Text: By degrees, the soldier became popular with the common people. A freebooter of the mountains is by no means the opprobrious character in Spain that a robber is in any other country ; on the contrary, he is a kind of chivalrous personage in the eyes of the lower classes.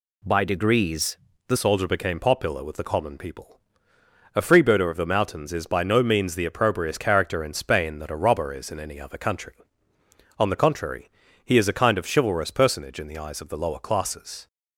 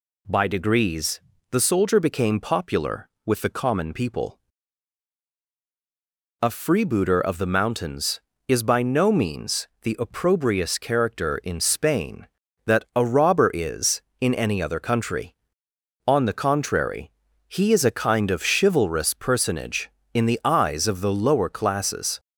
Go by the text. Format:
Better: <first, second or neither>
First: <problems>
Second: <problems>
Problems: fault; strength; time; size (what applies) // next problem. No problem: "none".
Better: second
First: changes voice at "soldier"; from 1.5 s on; 12.9 s long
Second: none